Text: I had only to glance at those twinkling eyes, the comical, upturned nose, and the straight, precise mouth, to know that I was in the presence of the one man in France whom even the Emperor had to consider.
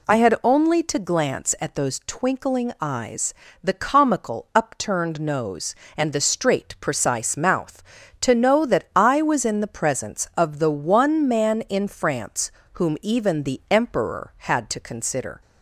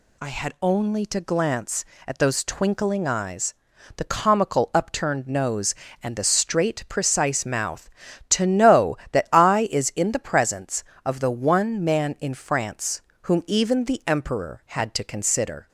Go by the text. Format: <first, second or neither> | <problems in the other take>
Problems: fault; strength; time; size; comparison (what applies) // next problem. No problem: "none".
first | says "is" for "was"; at 9.7 s // pauses between "France" and "whom"; slight; at 13.0 s; 0.22 s long; slight in the first